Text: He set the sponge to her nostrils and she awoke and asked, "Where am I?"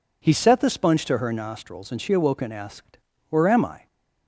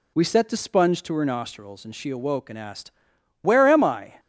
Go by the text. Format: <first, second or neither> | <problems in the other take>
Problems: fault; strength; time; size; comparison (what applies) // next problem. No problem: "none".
first | says "We" for "He"; at 0.1 s